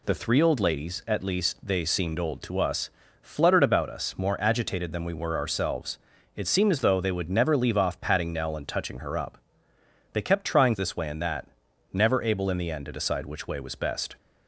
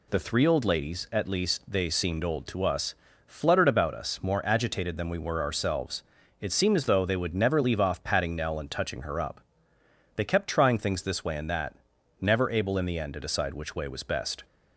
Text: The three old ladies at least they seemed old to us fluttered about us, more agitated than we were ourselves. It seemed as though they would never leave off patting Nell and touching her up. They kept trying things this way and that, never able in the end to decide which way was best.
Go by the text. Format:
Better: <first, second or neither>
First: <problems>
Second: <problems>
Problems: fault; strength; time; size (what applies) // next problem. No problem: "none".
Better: second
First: pauses between "us" and "fluttered"; slight; at 2.9 s; 0.32 s long // skips "things"; at 10.7 s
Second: pauses between "us" and "fluttered"; slight; at 2.9 s; 0.32 s long